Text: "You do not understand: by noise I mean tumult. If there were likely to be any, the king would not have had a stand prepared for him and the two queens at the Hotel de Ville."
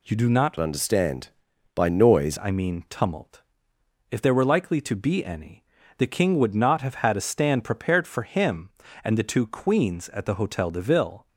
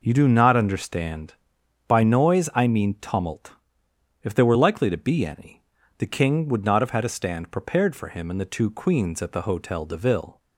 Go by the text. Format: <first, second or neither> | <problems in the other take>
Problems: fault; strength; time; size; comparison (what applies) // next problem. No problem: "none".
second | changes voice from "understand" to "noise"; from 0.5 to 2.3 s; 1.8 s long